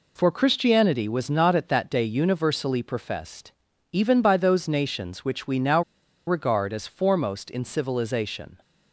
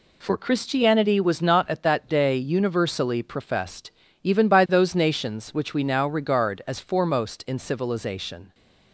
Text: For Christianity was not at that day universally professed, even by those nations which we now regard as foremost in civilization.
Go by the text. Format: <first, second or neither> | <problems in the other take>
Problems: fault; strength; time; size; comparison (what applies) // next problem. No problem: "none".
second | pauses between "now" and "regard"; at 5.8 s; 0.44 s long